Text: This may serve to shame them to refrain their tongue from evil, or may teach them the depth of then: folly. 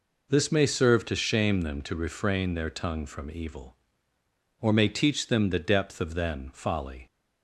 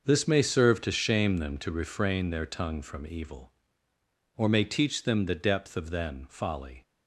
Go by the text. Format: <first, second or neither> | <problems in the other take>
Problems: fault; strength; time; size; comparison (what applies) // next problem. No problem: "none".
first | gets quieter; strong; throughout; 12 dB